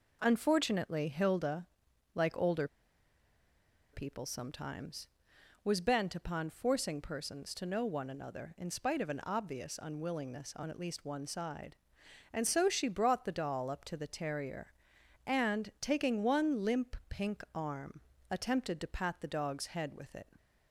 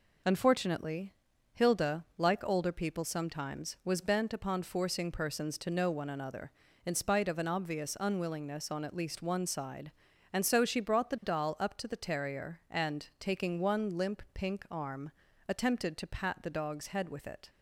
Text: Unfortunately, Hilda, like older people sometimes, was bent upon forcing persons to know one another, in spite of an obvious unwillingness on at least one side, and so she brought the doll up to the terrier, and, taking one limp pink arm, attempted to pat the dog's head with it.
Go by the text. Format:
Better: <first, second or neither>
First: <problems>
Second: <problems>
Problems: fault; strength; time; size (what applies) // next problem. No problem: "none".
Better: second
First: pauses between "older" and "people"; strong; at 2.6 s; 1.2 s long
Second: none